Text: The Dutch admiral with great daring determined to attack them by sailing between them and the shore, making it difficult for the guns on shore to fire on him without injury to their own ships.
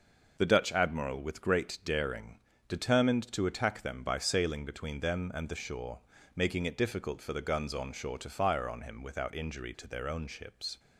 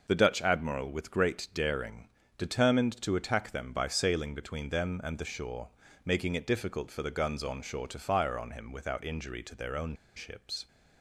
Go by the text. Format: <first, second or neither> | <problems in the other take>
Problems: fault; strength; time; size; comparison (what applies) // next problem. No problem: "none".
first | pauses between "daring" and "determined"; slight; at 2.0 s; 0.28 s long; slight in the first // pauses between "own" and "ships"; slight; at 9.9 s; 0.21 s long